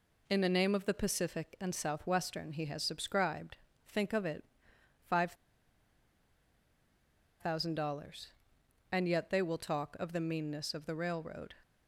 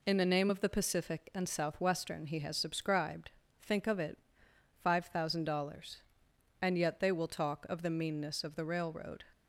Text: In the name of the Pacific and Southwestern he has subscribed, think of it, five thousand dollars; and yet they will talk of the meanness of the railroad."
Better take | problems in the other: second | pauses between "five" and "thousand"; strong; at 5.3 s; 2.0 s long

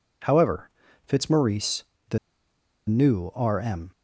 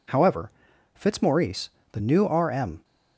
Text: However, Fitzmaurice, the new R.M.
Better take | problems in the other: second | pauses between "the" and "new"; noticeable; at 2.1 s; 0.70 s long

